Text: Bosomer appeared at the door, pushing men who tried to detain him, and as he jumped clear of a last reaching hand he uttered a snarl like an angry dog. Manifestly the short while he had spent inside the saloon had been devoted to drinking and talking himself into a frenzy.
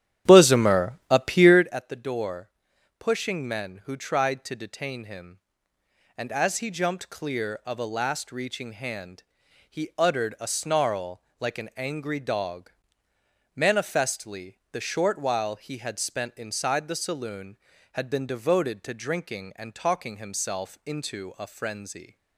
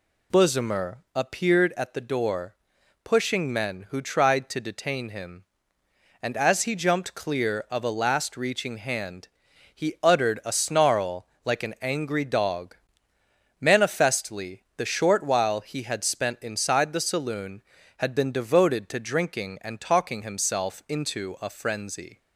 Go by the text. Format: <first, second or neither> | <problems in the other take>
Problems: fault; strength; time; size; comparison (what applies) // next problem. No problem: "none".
second | starts louder than the rest; strong; until 1.8 s; 11 dB // pauses between "hand" and "he"; noticeable; at 9.2 s; 0.48 s long; noticeable in the second // pauses between "snarl" and "like"; slight; at 11.2 s; 0.18 s long; slight in the second // pauses between "Manifestly" and "the"; slight; at 14.5 s; 0.16 s long; slight in the second